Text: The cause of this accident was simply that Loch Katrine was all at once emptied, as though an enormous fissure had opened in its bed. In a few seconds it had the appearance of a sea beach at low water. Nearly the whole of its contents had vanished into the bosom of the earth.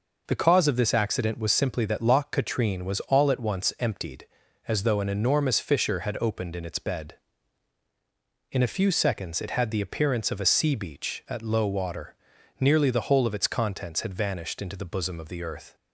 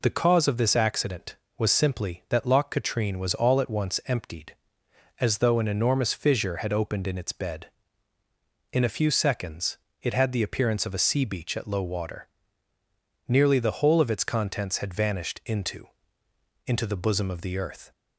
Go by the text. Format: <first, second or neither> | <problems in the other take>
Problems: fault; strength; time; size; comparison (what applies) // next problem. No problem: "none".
first | pauses between "seconds" and "it"; slight; at 9.7 s; 0.24 s long // says "into" twice; at 16.6 s